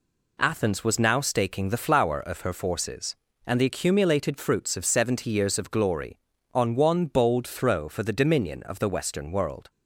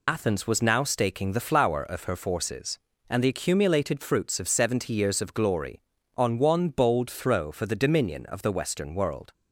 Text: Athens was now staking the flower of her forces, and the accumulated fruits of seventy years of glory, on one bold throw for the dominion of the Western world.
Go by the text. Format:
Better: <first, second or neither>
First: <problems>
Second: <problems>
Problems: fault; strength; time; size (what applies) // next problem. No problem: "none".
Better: first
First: none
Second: loses the start of "Athens"; at 0.0 s; 55 ms